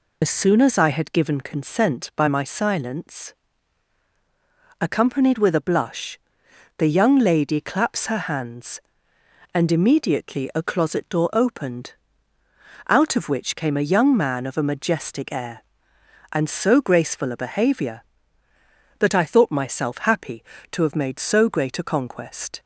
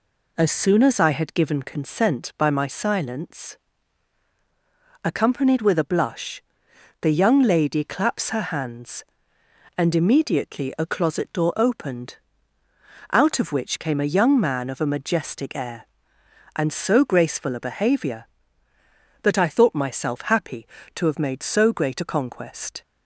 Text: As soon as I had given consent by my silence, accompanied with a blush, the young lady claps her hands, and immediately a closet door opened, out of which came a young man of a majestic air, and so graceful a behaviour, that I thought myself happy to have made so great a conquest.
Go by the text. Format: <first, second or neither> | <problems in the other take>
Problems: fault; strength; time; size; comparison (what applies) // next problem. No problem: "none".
second | loses the start of "As"; at 0.2 s; 65 ms